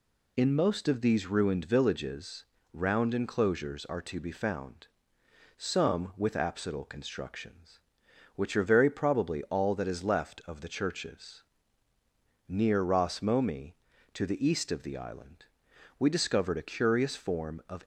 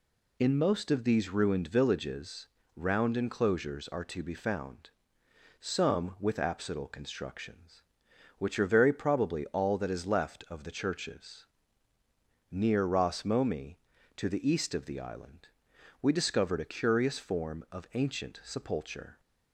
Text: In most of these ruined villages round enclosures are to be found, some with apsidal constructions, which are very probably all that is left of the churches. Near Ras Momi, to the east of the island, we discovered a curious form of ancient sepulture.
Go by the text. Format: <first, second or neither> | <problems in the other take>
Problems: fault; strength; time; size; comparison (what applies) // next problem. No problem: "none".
second | pauses between "villages" and "round"; slight; at 2.4 s; 0.28 s long; slight in the second // stops before "ancient sepulture"; at 17.8 s